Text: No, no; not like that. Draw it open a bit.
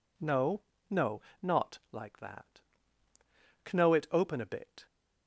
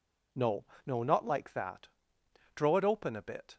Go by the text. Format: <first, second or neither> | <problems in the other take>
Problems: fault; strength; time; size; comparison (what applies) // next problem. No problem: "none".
second | says "Kno" for "Draw"; at 3.6 s